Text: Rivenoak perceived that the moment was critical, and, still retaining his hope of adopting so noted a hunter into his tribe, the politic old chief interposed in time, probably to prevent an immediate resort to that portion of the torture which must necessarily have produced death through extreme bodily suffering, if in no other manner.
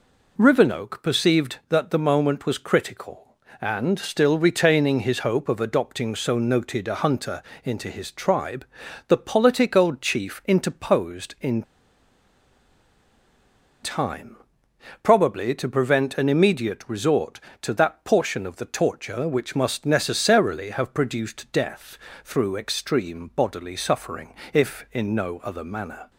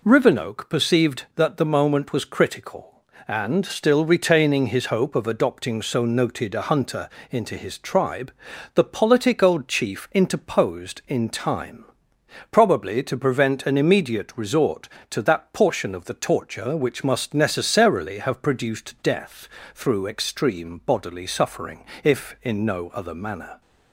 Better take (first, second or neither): second